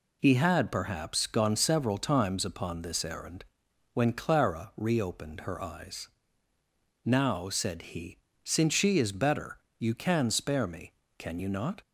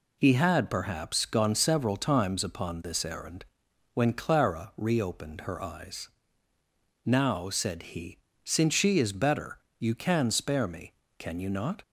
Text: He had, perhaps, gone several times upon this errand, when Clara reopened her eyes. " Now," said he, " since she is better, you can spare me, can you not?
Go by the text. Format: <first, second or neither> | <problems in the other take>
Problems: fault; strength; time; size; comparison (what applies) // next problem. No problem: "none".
neither | none